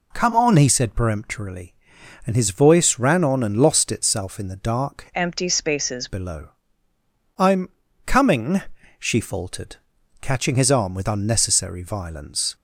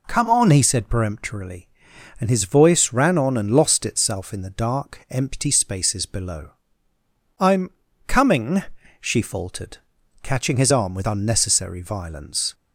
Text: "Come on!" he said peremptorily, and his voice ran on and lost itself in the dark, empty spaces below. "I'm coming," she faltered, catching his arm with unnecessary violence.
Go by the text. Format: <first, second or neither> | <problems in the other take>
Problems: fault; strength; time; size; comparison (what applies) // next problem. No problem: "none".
second | changes voice from "empty" to "spaces"; from 5.1 to 6.0 s; 0.9 s long // pauses between "I'm" and "coming"; at 7.6 s; 0.38 s long; also in the second